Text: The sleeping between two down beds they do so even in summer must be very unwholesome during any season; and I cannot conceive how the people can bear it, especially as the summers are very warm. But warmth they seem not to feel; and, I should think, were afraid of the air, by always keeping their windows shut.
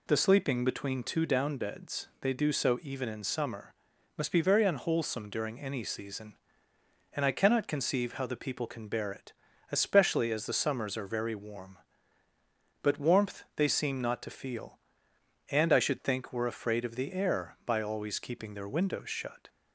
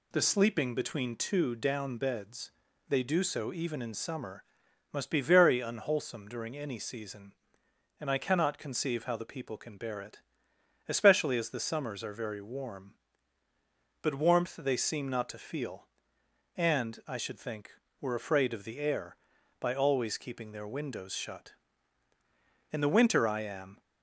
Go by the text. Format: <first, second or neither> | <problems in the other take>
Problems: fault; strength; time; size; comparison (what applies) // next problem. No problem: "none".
first | pauses between "beds" and "they"; at 2.5 s; 0.38 s long // pauses between "summer" and "must"; noticeable; at 4.4 s; 0.48 s long; also in the first // goes on to say "In the winter I am"; noticeable; from 22.7 s on; 1.0 s long